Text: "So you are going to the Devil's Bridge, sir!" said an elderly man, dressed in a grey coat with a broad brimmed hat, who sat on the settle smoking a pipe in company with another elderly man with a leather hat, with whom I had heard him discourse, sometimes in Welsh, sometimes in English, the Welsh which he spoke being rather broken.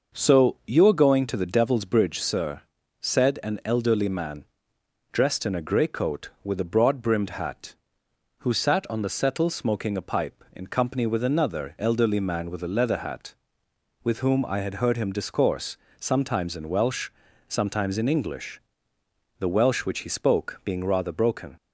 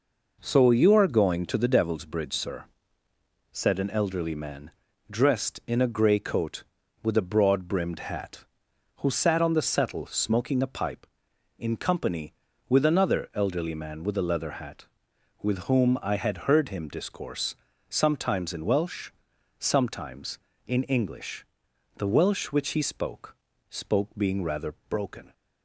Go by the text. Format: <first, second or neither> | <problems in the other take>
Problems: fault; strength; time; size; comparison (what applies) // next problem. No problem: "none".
first | says "spoke" twice; at 23.6 s // pauses between "rather" and "broken"; slight; at 24.7 s; 0.16 s long